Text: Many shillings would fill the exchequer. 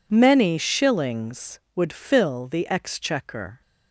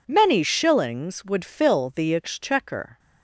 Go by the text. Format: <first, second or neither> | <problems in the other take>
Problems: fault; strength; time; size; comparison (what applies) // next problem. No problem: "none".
neither | none